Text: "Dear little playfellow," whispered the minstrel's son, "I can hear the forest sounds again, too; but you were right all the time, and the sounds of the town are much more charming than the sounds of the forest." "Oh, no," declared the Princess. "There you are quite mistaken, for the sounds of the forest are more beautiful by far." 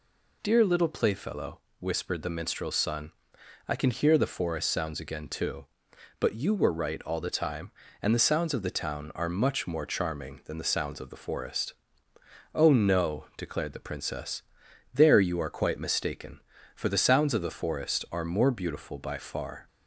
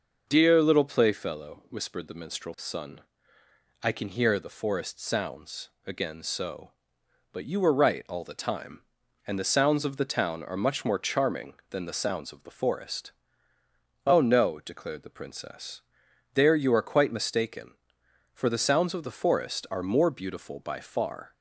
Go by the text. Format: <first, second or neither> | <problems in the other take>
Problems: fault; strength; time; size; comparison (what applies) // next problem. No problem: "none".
first | pauses between "sounds" and "again"; slight; at 5.6 s; 0.16 s long // says "so" for "too"; at 6.2 s